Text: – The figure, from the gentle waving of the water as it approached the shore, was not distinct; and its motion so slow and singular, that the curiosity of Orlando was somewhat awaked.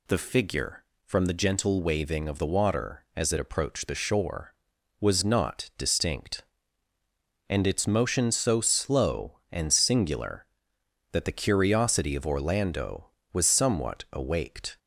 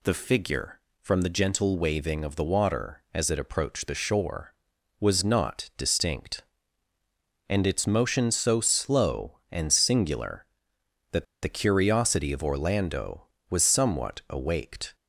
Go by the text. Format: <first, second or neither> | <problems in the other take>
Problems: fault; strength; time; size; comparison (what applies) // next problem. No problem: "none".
first | pauses between "that" and "the"; slight; at 11.2 s; 0.17 s long